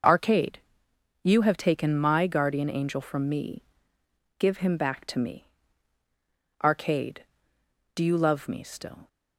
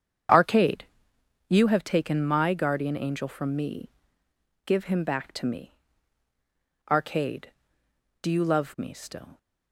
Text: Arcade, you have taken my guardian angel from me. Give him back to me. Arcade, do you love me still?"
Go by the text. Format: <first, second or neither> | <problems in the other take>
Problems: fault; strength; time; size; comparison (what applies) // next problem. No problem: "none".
first | starts louder than the rest; strong; until 1.8 s; 8 dB